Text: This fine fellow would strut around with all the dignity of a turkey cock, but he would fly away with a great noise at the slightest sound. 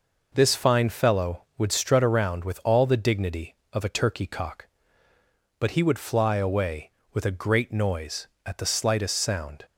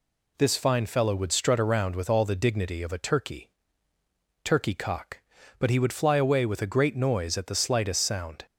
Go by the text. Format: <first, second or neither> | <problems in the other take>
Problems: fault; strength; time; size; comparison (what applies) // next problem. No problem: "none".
first | says "turkey" twice; at 4.4 s